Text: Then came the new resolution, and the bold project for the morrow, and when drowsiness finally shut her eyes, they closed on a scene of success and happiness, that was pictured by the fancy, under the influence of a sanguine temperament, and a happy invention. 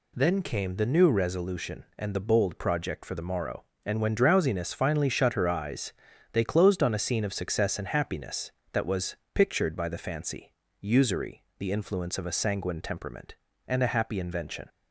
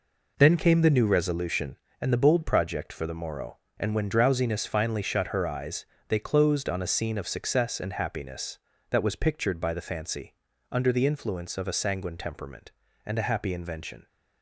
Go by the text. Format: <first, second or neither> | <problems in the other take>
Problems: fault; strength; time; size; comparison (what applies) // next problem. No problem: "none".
second | pauses between "was" and "pictured"; slight; at 9.1 s; 0.18 s long // says "usury" for "under"; at 10.8 s